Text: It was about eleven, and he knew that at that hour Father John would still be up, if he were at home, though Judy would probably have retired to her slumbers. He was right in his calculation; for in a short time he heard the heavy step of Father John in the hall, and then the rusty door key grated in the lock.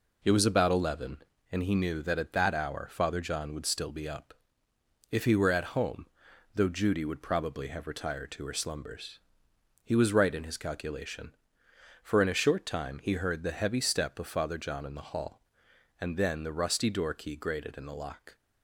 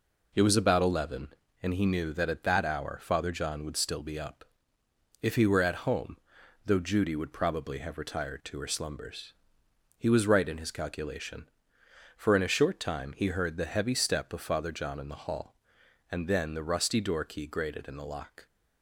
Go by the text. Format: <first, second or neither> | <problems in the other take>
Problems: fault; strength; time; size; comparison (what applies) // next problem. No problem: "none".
neither | none